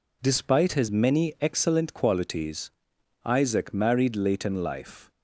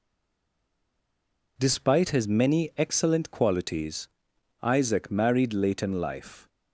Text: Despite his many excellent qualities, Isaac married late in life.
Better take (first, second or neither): first